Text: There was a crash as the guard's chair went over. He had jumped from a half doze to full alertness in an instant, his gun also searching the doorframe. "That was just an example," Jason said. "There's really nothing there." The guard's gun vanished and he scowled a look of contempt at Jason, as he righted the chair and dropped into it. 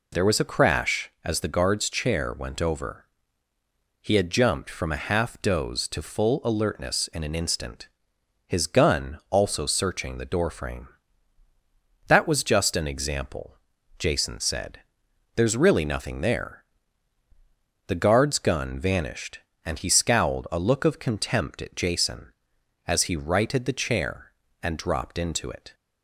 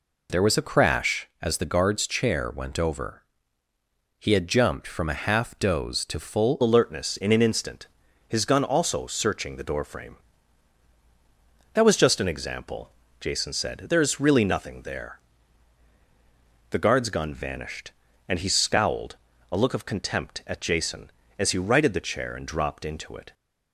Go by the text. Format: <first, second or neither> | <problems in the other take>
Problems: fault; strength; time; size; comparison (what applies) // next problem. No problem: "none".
first | changes voice at "alertness"; from 6.6 s on; 16.7 s long // pauses between "scowled" and "a"; slight; at 19.1 s; 0.34 s long